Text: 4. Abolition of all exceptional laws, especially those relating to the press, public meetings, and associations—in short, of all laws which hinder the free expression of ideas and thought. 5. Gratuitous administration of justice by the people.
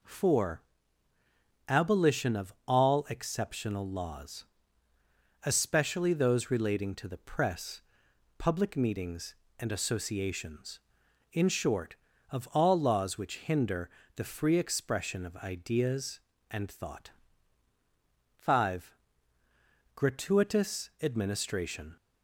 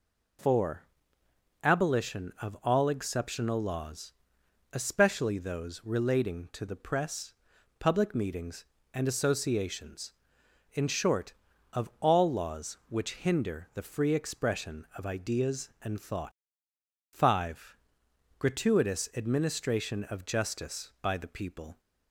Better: second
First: pauses between "of" and "all"; slight; at 2.5 s; 0.16 s long // pauses between "hinder" and "the"; slight; at 13.8 s; 0.28 s long // stops before "of justice by the people"; at 21.9 s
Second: none

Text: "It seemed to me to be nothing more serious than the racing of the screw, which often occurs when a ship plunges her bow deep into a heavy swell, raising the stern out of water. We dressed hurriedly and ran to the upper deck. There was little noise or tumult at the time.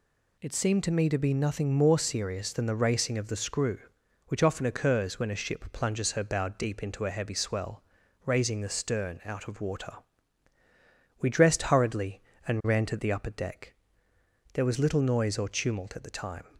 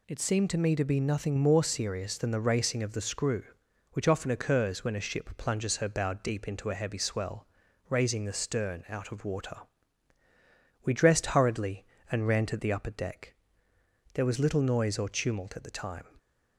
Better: neither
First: none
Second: none

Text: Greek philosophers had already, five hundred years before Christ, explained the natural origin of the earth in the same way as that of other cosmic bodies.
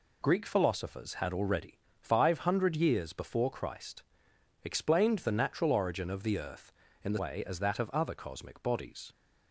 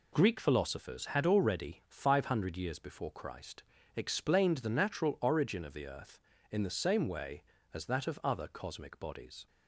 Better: second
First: skips "same"; at 7.1 s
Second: none

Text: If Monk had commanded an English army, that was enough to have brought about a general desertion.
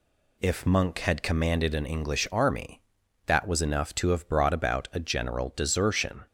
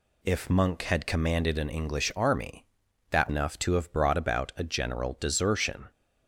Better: first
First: none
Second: skips "was"; at 3.2 s

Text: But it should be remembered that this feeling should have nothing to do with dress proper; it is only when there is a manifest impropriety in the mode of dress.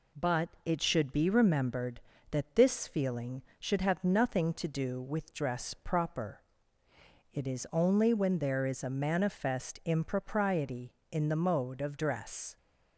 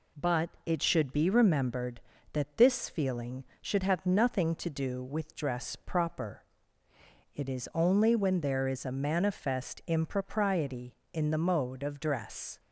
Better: neither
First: pauses between "But" and "it"; slight; at 0.4 s; 0.16 s long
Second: pauses between "But" and "it"; slight; at 0.4 s; 0.16 s long

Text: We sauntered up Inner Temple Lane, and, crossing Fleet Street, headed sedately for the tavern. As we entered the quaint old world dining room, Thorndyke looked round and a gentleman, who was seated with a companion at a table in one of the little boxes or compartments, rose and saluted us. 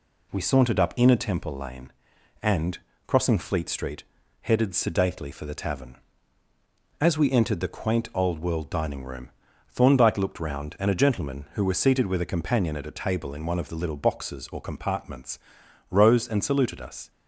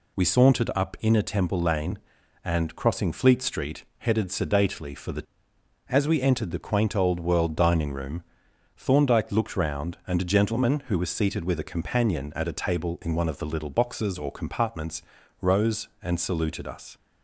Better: first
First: none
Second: skips "tavern"; at 5.5 s

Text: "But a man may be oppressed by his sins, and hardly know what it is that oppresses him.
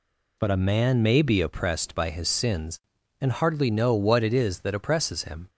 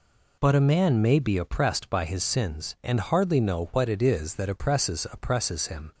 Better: first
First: none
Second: says "oppresses" twice; at 5.1 s

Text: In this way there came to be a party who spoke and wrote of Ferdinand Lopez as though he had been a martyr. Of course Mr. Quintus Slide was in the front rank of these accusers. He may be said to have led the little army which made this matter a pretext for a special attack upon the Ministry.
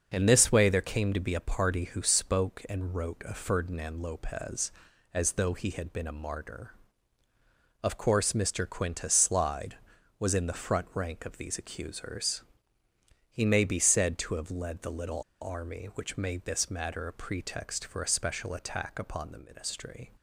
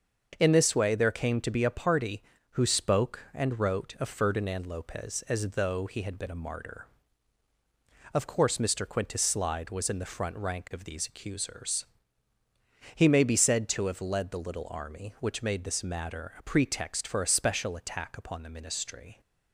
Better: second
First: starts louder than the rest; until 1.1 s; 6.5 dB // pauses between "little" and "army"; slight; at 15.2 s; 0.18 s long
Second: starts louder than the rest; until 1.4 s; 6.5 dB

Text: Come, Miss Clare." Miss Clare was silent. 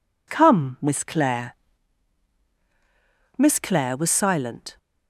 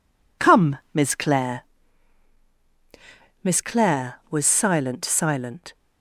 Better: first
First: none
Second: says "silent" twice; at 5.0 s

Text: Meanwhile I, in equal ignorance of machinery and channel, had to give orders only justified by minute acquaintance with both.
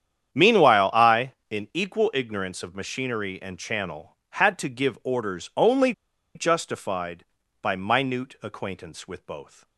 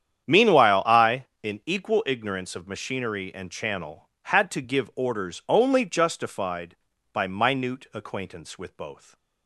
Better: second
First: starts louder than the rest; strong; until 1.5 s; 9 dB // pauses between "only" and "justified"; at 5.9 s; 0.43 s long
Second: starts louder than the rest; strong; until 1.4 s; 9 dB

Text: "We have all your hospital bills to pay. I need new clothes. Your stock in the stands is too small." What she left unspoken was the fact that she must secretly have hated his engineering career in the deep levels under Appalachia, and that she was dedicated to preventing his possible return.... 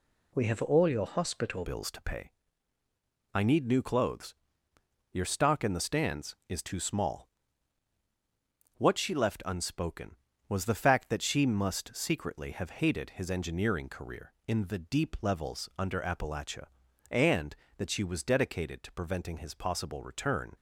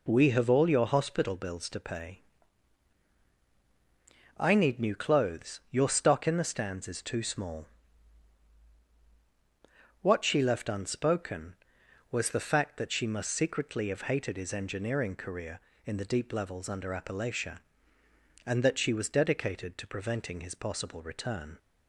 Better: second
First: changes voice at "bills"; from 1.6 s on; 18.9 s long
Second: none

